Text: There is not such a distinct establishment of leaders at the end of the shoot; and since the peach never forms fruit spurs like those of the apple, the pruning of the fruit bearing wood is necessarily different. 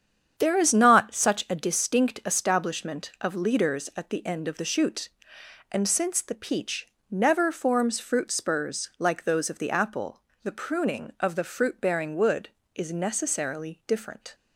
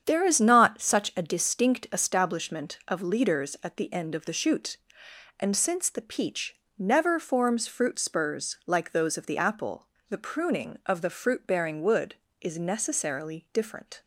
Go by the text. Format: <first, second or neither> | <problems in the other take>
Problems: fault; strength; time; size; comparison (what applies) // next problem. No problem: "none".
neither | starts louder than the rest; strong; the same in both // pauses between "peach" and "never"; slight; the same in both